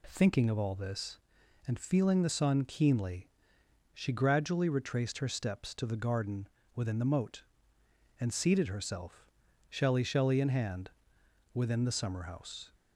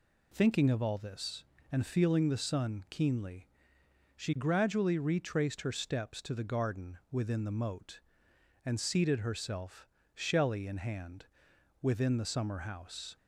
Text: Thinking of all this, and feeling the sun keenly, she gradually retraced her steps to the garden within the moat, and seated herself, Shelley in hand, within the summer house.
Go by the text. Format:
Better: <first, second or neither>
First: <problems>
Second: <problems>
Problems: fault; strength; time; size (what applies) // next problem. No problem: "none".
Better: second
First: pauses between "garden" and "within"; slight; at 6.4 s; 0.26 s long // says "Shelley" twice; at 10.0 s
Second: none